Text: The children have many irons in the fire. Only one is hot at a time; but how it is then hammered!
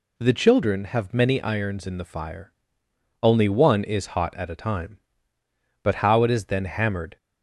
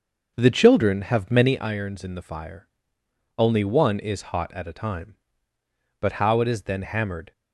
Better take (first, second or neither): first